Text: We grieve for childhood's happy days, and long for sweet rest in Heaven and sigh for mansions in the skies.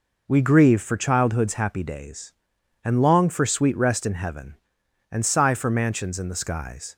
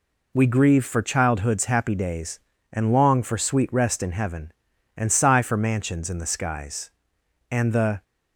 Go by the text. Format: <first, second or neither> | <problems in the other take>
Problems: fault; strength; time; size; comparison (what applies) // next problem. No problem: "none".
first | goes on to say "And the"; from 7.4 s on; 0.54 s long